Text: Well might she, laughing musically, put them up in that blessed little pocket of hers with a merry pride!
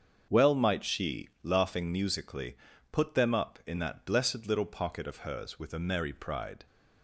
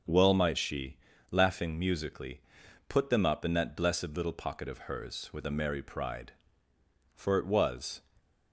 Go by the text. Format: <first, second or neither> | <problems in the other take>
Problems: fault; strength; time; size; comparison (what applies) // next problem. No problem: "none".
first | starts louder than the rest; noticeable; until 1.3 s; 6 dB; also in the first // goes on to say "For it was"; noticeable; from 7.1 s on; 0.88 s long // stays silent after the last word; slight; from 7.9 s on; 0.6 s long